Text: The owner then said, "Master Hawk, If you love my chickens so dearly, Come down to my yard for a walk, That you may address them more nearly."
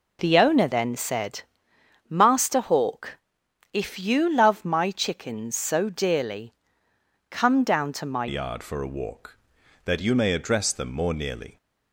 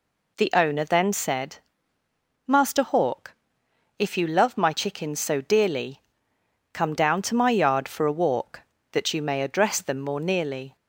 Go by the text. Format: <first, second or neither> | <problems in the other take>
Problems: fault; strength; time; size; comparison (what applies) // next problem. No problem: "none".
second | changes voice at "yard"; from 8.2 s on; 3.3 s long